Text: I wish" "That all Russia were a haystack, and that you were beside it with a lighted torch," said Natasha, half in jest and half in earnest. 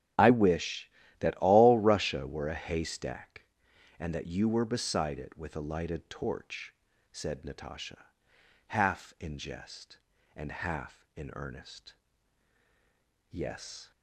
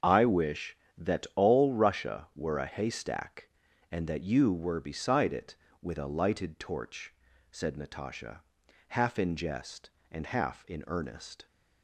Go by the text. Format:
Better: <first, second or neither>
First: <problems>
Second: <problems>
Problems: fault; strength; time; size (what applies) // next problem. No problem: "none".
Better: second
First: starts louder than the rest; strong; until 1.4 s; 9.5 dB // goes on to say "Yes"; from 13.3 s on; 0.60 s long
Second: starts louder than the rest; until 1.2 s; 6.5 dB